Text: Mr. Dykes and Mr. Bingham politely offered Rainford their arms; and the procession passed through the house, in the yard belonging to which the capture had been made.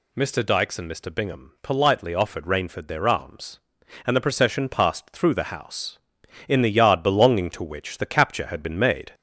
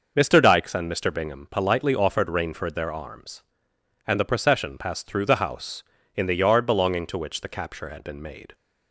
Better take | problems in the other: second | gets louder; throughout; 3.5 dB

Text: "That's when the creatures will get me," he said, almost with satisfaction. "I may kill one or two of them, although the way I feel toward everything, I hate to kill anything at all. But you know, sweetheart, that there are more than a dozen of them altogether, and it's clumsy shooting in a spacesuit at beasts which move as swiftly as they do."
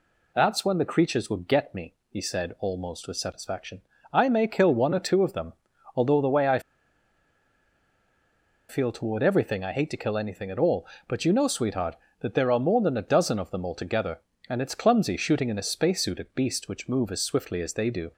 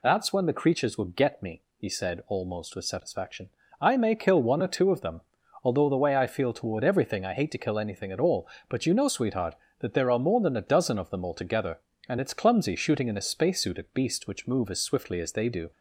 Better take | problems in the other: second | pauses between "I" and "feel"; strong; at 6.5 s; 2.0 s long

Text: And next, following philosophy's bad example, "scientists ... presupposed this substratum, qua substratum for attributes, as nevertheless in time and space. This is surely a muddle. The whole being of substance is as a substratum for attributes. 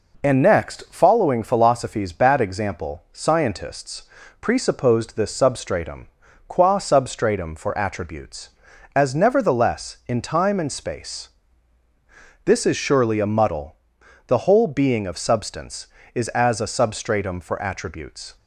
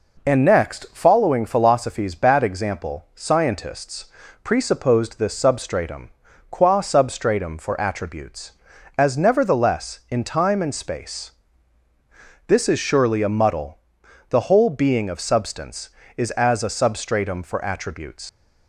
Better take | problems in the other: first | leaves "attributes" unfinished; at 18.2 s; 90 ms

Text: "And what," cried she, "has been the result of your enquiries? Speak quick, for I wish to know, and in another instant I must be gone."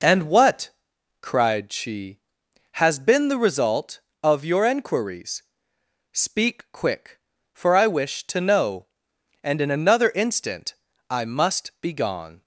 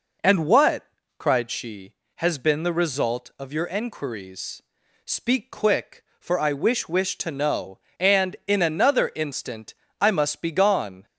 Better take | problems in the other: first | says "wish" twice; at 6.8 s // pauses between "instant" and "I"; slight; at 9.7 s; 0.26 s long; slight in the first

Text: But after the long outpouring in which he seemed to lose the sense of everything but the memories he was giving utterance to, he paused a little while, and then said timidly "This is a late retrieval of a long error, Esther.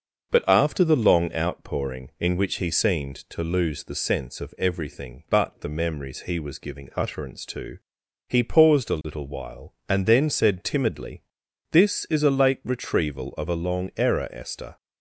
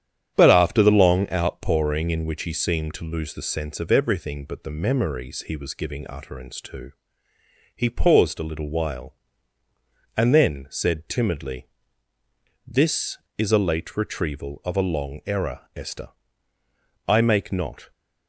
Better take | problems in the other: first | starts louder than the rest; strong; until 1.3 s; 9.5 dB; noticeable in the first // pauses between "timidly" and "This"; at 11.6 s; 1.0 s long; noticeable in the first // goes on to say "I make not"; noticeable; from 17.0 s on; 0.84 s long

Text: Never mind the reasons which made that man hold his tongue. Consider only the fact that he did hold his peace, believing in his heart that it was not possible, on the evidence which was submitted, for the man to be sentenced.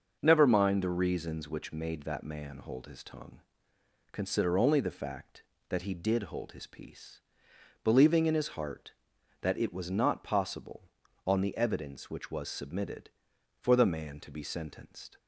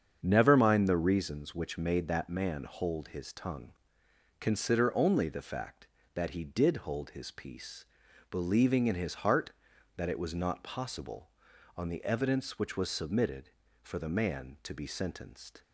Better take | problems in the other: neither | starts louder than the rest; the same in both

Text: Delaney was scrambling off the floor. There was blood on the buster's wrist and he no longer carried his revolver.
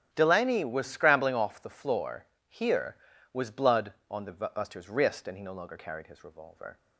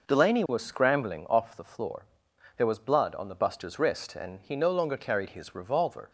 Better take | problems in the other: second | starts louder than the rest; strong; until 1.1 s; 10.5 dB // says "Here" for "There"; at 2.4 s

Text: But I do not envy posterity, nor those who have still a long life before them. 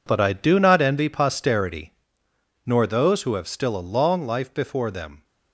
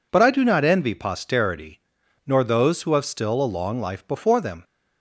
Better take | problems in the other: second | gets quieter; strong; throughout; 12 dB

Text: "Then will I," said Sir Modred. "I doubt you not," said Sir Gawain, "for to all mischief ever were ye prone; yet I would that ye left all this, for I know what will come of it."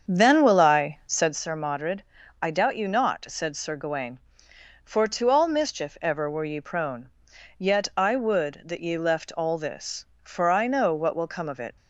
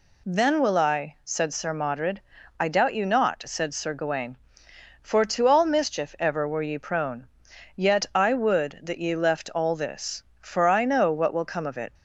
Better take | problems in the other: second | starts louder than the rest; strong; until 1.4 s; 7 dB

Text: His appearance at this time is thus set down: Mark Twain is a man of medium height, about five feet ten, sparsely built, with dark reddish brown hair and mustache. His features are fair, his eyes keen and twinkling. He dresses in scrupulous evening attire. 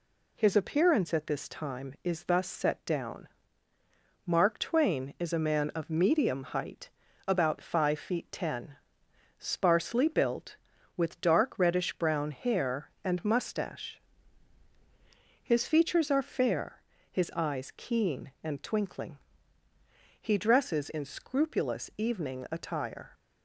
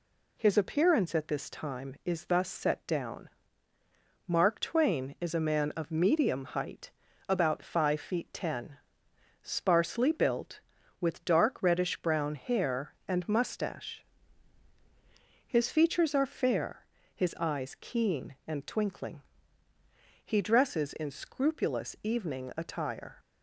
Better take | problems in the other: neither | none

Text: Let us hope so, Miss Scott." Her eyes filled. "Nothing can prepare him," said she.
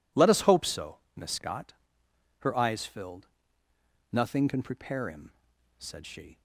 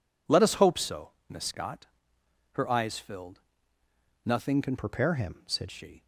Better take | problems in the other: first | changes voice from "prepare" to "said"; from 4.7 to 5.6 s; 0.9 s long

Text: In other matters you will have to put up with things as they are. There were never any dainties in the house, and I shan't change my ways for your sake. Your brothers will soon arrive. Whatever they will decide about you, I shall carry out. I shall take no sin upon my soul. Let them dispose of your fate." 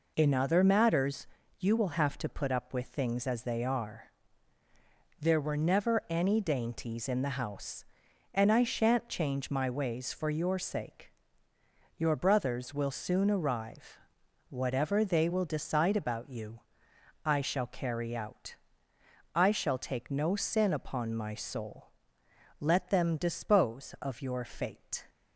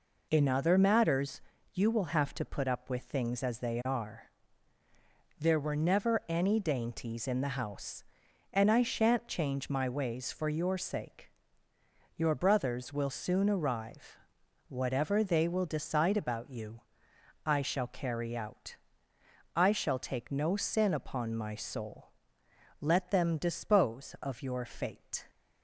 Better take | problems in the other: neither | pauses between "matters" and "you"; slight; the same in both

